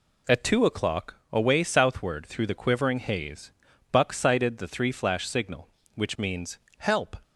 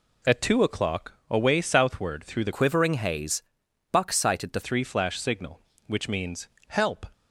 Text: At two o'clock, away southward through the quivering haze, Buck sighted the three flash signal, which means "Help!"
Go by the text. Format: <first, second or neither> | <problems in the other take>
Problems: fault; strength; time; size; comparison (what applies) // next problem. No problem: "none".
first | changes voice from "quivering" to "the"; from 2.5 to 4.6 s; 2.1 s long // pauses between "means" and "Help"; slight; at 6.4 s; 0.20 s long; slight in the first